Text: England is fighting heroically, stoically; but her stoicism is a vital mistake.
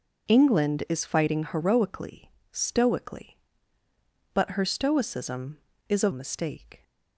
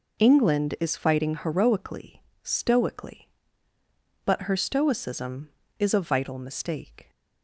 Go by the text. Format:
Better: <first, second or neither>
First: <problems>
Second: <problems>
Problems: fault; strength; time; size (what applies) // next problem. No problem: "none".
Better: second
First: skips "vital"; at 6.1 s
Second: none